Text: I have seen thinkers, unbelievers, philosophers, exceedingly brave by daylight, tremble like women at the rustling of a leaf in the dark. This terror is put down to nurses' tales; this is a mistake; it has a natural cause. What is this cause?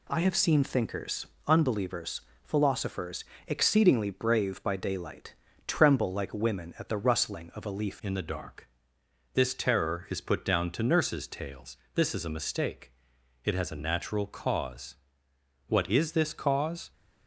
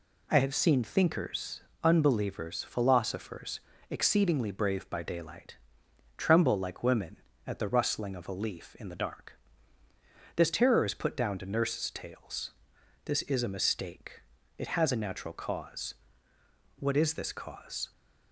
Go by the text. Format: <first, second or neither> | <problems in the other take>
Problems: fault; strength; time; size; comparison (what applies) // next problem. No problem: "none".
second | changes voice at "in"; from 8.0 s on; 8.9 s long